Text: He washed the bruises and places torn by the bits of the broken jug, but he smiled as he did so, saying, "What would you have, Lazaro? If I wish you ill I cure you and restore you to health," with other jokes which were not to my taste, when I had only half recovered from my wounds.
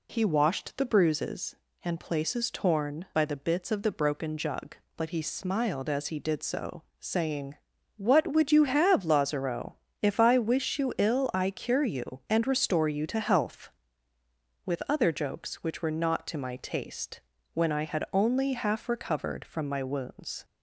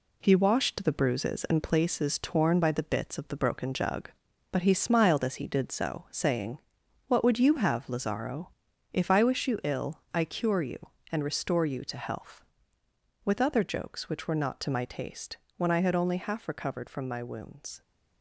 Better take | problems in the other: first | gets quieter; noticeable; throughout; 5.5 dB

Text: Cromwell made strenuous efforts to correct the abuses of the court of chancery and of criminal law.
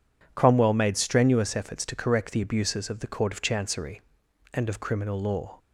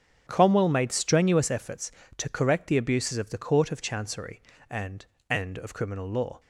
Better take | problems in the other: first | starts louder than the rest; strong; until 1.2 s; 8 dB // says "and" twice; at 5.2 s

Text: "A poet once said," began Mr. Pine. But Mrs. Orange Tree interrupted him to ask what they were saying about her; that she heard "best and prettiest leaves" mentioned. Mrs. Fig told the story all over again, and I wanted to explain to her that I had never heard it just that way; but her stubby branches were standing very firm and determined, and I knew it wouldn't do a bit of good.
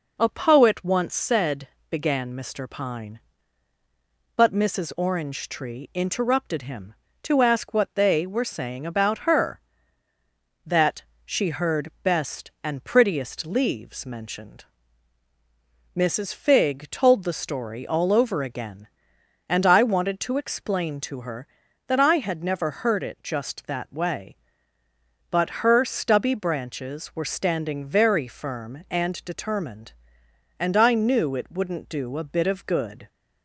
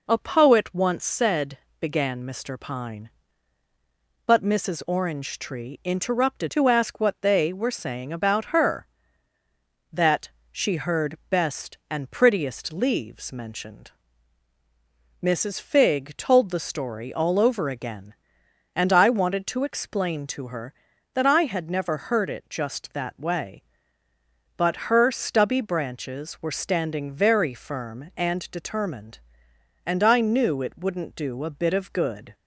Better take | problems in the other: first | skips "him"; at 6.4 s // pauses between "that" and "she"; slight; at 10.2 s; 0.22 s long; slight in the first

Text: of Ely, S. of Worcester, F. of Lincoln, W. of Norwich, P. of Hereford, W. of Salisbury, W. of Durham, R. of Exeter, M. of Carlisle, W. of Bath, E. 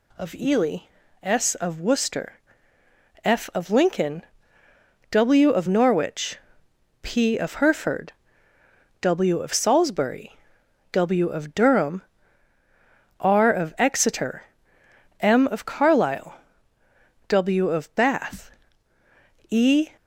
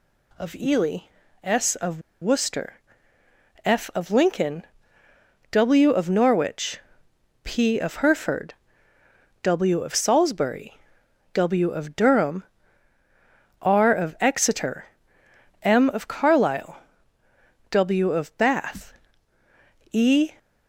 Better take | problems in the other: first | pauses between "of" and "Worcester"; slight; at 1.9 s; 0.21 s long

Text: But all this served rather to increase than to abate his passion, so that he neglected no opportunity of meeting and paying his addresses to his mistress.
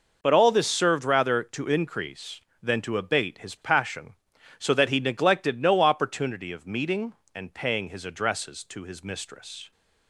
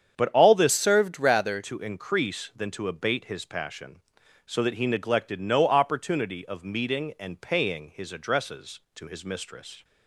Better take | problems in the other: first | starts louder than the rest; strong; until 1.2 s; 8 dB // changes voice from "served" to "rather"; from 0.7 to 1.6 s; 0.9 s long

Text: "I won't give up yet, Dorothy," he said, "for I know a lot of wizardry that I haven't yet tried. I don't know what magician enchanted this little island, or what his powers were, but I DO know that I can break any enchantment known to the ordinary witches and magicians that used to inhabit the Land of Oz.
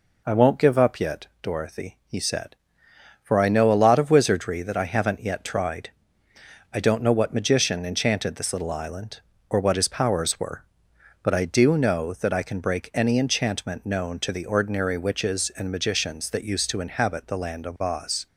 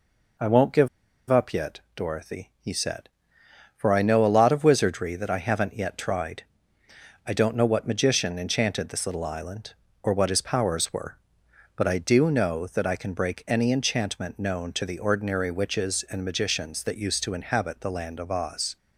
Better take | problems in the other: first | pauses between "give" and "up"; at 0.8 s; 0.42 s long

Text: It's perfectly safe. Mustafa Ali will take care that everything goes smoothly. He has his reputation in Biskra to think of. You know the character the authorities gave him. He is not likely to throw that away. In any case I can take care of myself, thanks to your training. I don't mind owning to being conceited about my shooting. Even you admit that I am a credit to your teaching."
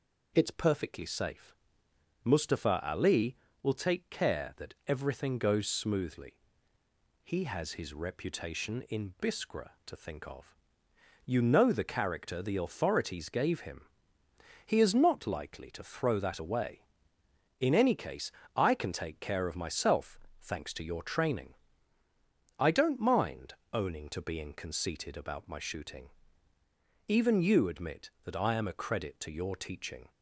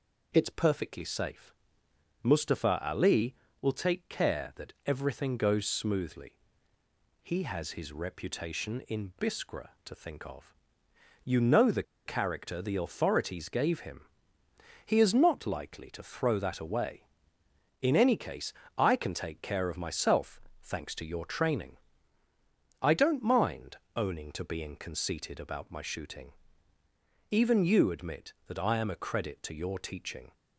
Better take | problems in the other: first | pauses between "the" and "character"; slight; at 11.8 s; 0.23 s long // pauses between "case" and "I"; slight; at 18.5 s; 0.24 s long; slight in the first // pauses between "mind" and "owning"; slight; at 23.7 s; 0.18 s long; slight in the first

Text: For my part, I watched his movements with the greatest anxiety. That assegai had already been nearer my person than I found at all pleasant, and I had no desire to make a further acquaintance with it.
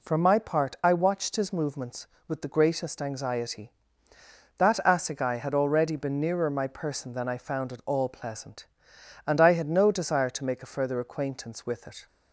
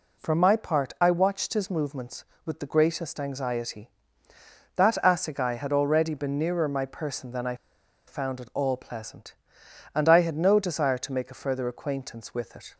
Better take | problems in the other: first | pauses between "I" and "found"; noticeable; at 7.5 s; 0.52 s long

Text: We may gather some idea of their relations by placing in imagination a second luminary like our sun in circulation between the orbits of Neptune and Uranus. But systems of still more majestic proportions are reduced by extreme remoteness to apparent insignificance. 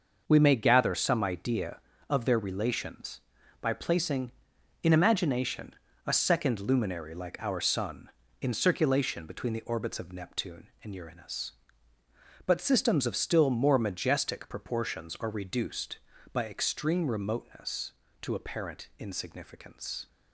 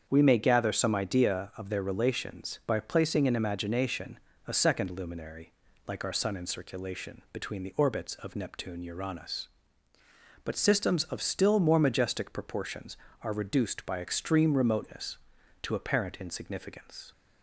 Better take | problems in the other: first | starts louder than the rest; strong; until 1.1 s; 7 dB; noticeable in the first // pauses between "imagination" and "a"; slight; at 4.1 s; 0.28 s long; slight in the first // pauses between "luminary" and "like"; slight; at 5.5 s; 0.34 s long // skips "and"; at 8.8 s

